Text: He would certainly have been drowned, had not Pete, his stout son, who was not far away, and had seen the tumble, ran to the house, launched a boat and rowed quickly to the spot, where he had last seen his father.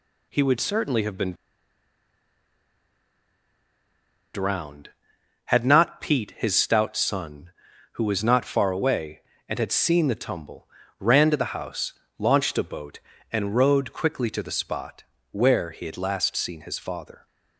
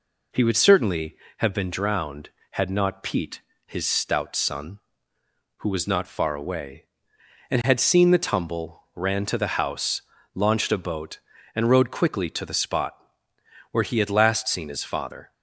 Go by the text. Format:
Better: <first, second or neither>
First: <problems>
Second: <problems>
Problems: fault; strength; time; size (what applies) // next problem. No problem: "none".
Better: second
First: pauses between "been" and "drowned"; strong; at 1.3 s; 3.0 s long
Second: none